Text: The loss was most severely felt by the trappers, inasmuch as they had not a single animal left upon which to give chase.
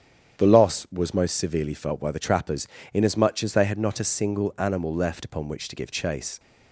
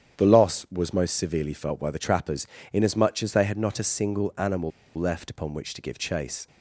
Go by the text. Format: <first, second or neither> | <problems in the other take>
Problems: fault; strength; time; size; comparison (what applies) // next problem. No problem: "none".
first | starts louder than the rest; strong; until 1.2 s; 9 dB; strong in the first // pauses between "animal" and "left"; slight; at 4.7 s; 0.27 s long